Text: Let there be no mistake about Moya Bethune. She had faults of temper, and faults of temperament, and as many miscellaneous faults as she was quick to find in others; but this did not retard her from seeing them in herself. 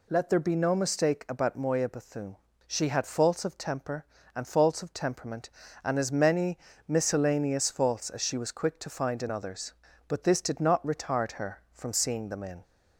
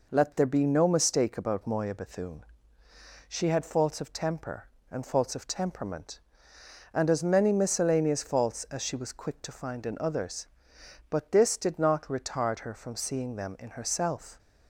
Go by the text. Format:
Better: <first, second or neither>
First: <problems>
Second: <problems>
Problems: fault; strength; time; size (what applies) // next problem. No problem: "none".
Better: second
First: pauses between "many" and "miscellaneous"; slight; at 6.5 s; 0.30 s long // stops before "herself"; at 12.6 s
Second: none